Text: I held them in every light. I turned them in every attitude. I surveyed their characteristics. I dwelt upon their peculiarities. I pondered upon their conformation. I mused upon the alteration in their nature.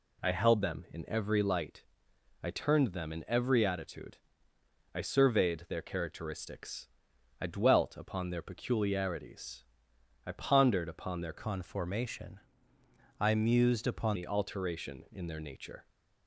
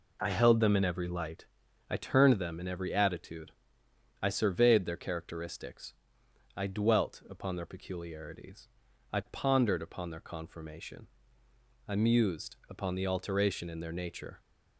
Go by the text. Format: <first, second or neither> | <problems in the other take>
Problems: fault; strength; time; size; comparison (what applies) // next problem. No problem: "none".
second | changes voice from "conformation" to "upon"; from 11.3 to 14.1 s; 2.8 s long